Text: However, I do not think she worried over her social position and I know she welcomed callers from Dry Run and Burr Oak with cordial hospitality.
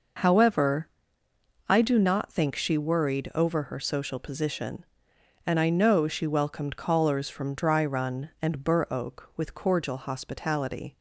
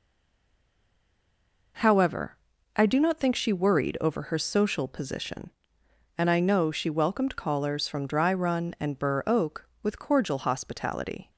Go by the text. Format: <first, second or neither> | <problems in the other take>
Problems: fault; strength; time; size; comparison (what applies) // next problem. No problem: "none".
first | stays silent before the first word; noticeable; until 1.7 s; 1.7 s long